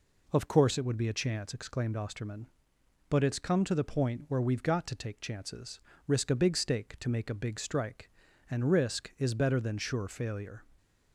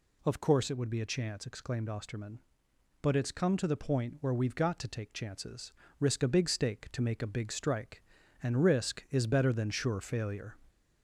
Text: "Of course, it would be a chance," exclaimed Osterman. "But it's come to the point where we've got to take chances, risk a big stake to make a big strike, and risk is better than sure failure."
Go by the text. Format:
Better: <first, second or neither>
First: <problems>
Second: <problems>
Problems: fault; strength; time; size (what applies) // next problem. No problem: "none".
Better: first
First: none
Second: gets louder; slight; throughout; 2.5 dB